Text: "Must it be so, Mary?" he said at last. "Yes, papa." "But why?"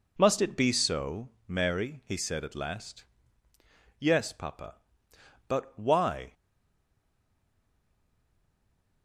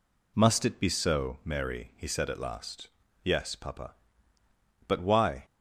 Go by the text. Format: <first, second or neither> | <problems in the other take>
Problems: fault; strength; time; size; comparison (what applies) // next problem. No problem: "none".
second | stays silent after the last word; strong; from 6.3 s on; 2.7 s long